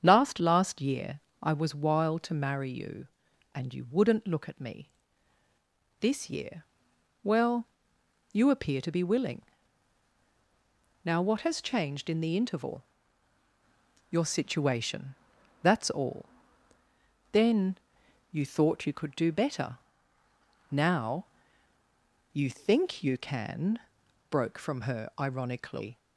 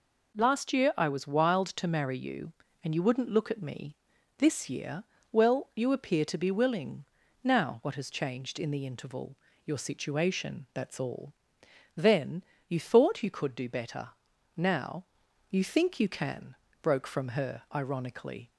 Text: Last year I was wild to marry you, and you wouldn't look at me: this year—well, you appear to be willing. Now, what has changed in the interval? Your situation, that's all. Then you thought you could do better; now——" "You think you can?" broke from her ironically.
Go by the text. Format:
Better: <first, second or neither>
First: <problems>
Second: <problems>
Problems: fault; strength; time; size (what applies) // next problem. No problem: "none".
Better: second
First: starts louder than the rest; strong; until 1.0 s; 8 dB // says "Last" twice; at 0.4 s // pauses between "year" and "I"; slight; at 1.2 s; 0.22 s long // pauses between "Then" and "you"; noticeable; at 17.7 s; 0.54 s long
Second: pauses between "Then" and "you"; slight; at 12.4 s; 0.24 s long